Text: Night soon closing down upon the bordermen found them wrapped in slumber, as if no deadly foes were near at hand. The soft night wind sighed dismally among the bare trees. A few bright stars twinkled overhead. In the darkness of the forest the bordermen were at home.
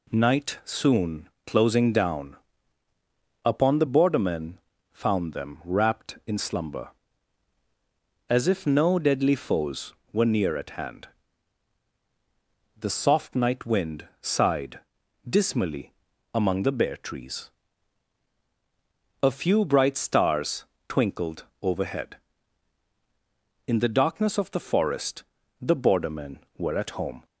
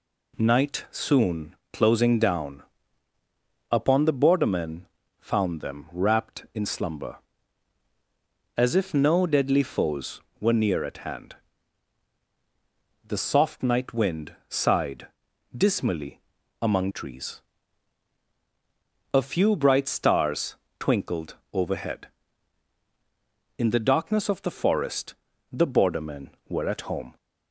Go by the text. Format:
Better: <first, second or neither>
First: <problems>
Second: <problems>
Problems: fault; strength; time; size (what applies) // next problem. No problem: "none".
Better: first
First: pauses between "soon" and "closing"; slight; at 1.2 s; 0.18 s long // pauses between "down" and "upon"; at 2.3 s; 1.0 s long // pauses between "bordermen" and "found"; slight; at 4.5 s; 0.34 s long // pauses between "sighed" and "dismally"; noticeable; at 14.7 s; 0.50 s long // pauses between "dismally" and "among"; at 15.9 s; 0.42 s long // pauses between "stars" and "twinkled"; slight; at 20.6 s; 0.24 s long // pauses between "twinkled" and "overhead"; slight; at 21.4 s; 0.18 s long // pauses between "forest" and "the"; slight; at 25.2 s; 0.36 s long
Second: pauses between "soon" and "closing"; slight; at 1.5 s; 0.18 s long // pauses between "down" and "upon"; at 2.6 s; 1.0 s long // pauses between "bordermen" and "found"; slight; at 4.8 s; 0.34 s long // pauses between "sighed" and "dismally"; noticeable; at 15.0 s; 0.50 s long // pauses between "dismally" and "among"; at 16.1 s; 0.42 s long // skips "the bare"; at 16.9 s // pauses between "stars" and "twinkled"; slight; at 20.5 s; 0.24 s long // pauses between "twinkled" and "overhead"; slight; at 21.3 s; 0.18 s long // pauses between "forest" and "the"; slight; at 25.1 s; 0.36 s long